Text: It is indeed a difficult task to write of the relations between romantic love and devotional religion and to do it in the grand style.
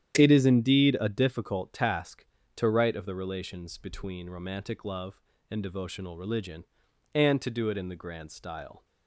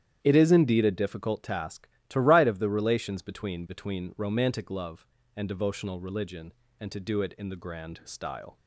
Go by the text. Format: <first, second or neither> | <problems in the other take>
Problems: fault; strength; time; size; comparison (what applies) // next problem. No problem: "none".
first | starts louder than the rest; strong; until 1.2 s; 10 dB; strong in the first // says "between" twice; at 3.6 s